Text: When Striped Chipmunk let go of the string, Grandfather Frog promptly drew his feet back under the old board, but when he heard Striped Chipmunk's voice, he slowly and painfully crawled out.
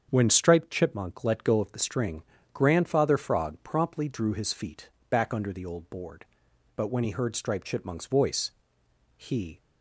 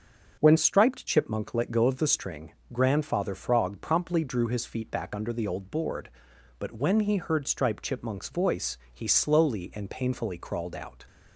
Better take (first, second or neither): second